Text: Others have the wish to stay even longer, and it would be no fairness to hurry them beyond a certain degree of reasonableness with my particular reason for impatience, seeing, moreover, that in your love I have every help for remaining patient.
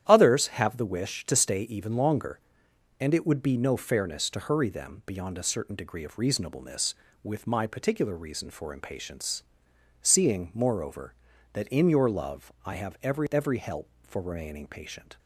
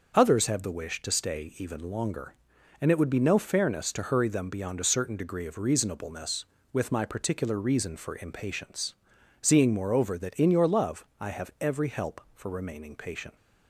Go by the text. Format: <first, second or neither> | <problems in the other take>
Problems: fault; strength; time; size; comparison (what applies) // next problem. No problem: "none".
second | starts louder than the rest; strong; until 1.0 s; 10.5 dB; also in the second // says "every" twice; at 13.2 s